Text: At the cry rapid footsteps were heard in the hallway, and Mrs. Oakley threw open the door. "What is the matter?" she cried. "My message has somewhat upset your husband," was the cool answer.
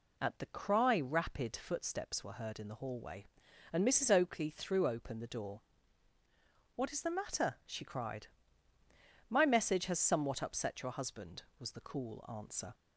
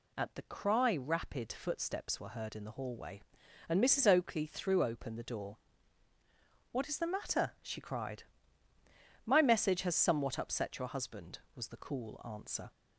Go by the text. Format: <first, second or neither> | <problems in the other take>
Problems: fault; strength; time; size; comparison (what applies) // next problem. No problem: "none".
second | starts louder than the rest; slight; until 1.6 s; 3 dB